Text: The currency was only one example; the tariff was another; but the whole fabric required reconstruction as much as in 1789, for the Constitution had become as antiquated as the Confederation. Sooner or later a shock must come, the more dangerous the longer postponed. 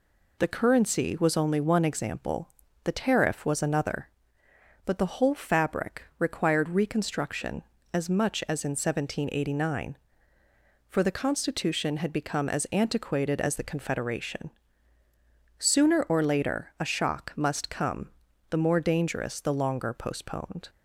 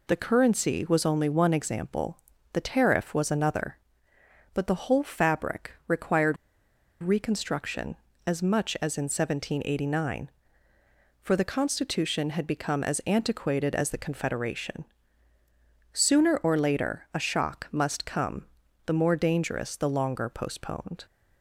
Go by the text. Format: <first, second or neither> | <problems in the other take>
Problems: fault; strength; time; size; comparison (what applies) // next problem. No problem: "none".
first | pauses between "fabric" and "required"; slight; at 5.7 s; 0.16 s long; slight in the first // pauses between "required" and "reconstruction"; noticeable; at 6.3 s; 0.66 s long